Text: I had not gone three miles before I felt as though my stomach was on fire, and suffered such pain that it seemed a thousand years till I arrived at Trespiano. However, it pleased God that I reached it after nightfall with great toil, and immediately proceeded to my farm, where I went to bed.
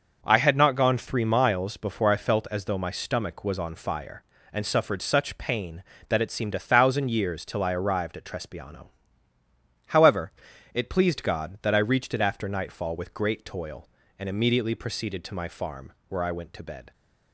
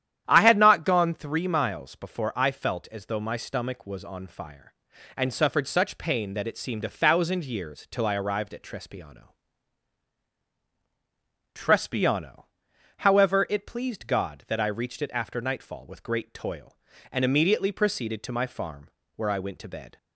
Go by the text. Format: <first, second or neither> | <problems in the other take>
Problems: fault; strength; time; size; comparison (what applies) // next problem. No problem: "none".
first | starts louder than the rest; strong; until 1.2 s; 10.5 dB; also in the first // says "Trespiano" twice; at 11.5 s